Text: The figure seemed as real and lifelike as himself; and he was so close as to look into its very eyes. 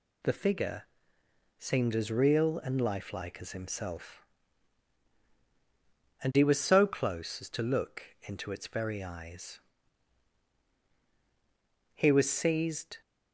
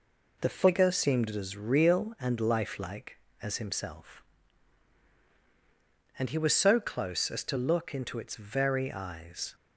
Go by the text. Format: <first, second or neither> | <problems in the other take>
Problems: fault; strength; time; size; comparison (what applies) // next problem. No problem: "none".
second | pauses between "figure" and "seemed"; noticeable; at 0.8 s; 0.74 s long // goes on to say "He was seized"; noticeable; from 11.9 s on; 1.0 s long